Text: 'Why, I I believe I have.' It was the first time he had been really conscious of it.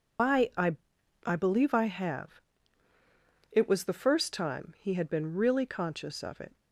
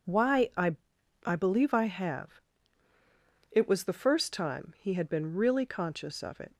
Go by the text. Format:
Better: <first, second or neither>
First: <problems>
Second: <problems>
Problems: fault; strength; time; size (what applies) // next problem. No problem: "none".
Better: second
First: loses the start of "Why"; at 0.1 s; 140 ms // pauses between "I" and "I"; noticeable; at 0.7 s; 0.50 s long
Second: pauses between "I" and "I"; noticeable; at 0.7 s; 0.50 s long